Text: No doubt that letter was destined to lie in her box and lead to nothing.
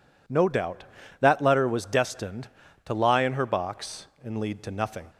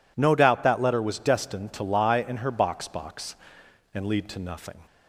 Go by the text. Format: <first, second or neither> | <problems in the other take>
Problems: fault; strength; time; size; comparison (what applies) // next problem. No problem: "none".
first | says "box" twice; at 2.8 s